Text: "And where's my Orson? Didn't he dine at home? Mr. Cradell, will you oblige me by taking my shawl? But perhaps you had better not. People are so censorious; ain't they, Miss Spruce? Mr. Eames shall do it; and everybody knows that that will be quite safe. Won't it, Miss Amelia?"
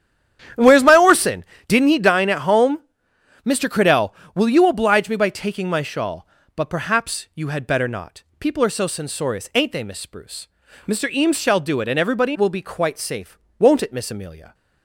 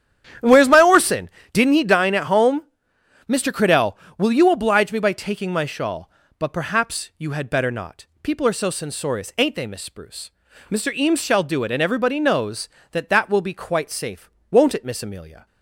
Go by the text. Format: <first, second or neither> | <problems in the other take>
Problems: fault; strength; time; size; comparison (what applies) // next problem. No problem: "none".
second | starts louder than the rest; strong; until 1.8 s; 10 dB; strong in the second // skips "knows that that"; at 12.3 s